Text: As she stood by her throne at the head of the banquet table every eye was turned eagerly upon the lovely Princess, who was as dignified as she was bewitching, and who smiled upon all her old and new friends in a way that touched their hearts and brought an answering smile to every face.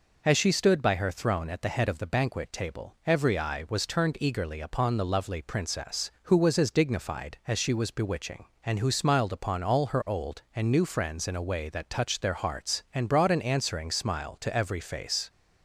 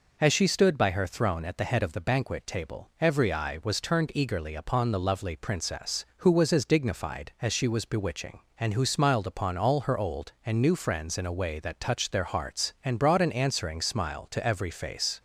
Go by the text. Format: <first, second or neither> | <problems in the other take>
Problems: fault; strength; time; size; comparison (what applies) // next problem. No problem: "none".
neither | none